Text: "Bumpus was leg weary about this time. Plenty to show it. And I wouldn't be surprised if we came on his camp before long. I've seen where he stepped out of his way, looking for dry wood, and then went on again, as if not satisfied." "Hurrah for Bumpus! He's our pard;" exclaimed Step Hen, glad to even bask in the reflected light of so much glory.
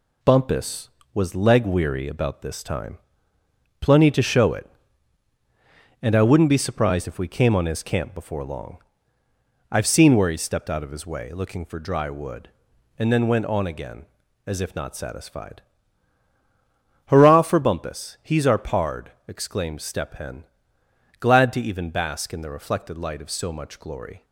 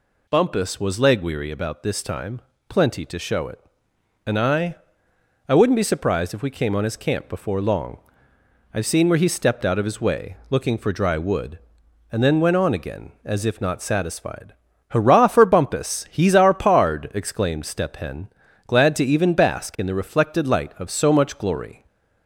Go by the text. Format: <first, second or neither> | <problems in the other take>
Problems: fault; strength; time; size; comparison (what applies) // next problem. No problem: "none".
first | says "I" twice; at 5.4 s // stays silent after the last word; slight; from 21.7 s on; 0.5 s long